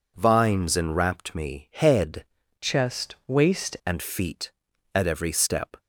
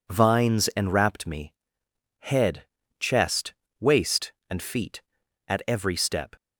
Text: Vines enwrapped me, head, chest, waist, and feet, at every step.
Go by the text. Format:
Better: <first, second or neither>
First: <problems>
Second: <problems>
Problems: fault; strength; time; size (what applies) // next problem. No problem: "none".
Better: second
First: changes voice from "chest" to "waist"; from 2.6 to 3.7 s; 1.1 s long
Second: none